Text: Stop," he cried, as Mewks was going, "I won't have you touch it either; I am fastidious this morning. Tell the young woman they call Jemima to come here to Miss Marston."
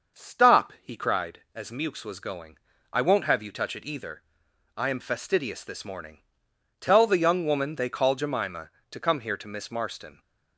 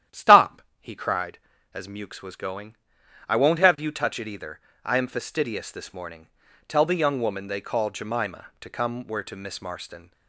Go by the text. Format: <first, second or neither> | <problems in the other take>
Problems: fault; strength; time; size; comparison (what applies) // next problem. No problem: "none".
first | starts louder than the rest; strong; until 1.3 s; 11 dB; also in the first // says "where" for "here"; at 9.0 s